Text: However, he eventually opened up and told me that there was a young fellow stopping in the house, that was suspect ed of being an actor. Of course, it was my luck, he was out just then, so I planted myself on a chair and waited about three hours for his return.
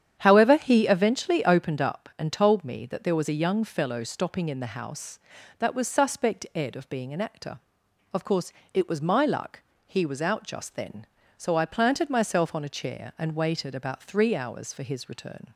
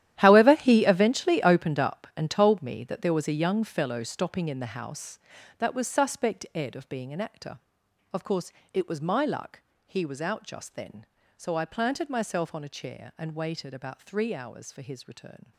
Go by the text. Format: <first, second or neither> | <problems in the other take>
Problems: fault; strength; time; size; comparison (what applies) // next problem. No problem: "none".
first | gets quieter; strong; throughout; 15 dB // starts louder than the rest; strong; until 1.2 s; 12 dB; strong in the first